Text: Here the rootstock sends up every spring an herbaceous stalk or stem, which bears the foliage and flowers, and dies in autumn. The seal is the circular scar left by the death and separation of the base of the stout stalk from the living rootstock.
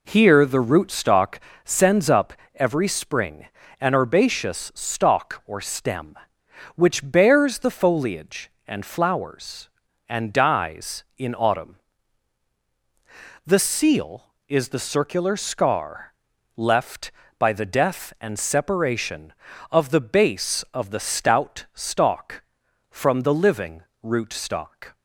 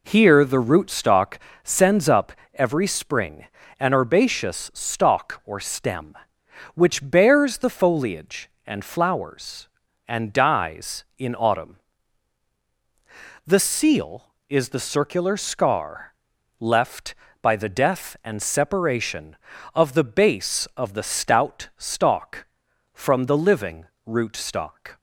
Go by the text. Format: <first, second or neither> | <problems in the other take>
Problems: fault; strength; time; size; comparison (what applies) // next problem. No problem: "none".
neither | pauses between "rootstock" and "sends"; slight; the same in both // pauses between "up" and "every"; slight; the same in both // pauses between "spring" and "an"; slight; the same in both // pauses between "scar" and "left"; the same in both // pauses between "living" and "rootstock"; slight; the same in both